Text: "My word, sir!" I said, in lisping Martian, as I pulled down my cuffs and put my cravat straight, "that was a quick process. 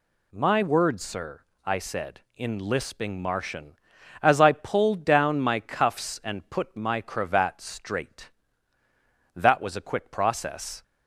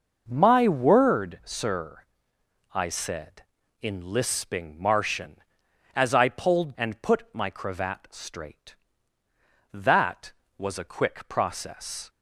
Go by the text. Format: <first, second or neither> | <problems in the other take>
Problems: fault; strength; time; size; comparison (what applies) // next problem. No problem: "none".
first | skips "down my cuffs"; at 6.7 s